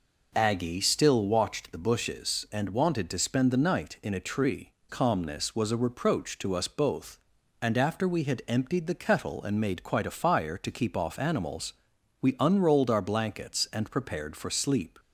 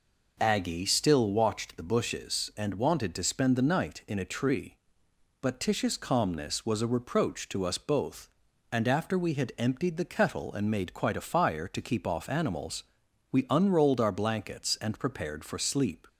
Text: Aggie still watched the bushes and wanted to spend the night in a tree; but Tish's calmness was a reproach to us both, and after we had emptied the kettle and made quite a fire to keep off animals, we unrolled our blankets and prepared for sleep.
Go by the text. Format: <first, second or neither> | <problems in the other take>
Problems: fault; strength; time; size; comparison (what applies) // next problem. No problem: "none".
second | skips "but Tish's"; at 4.8 s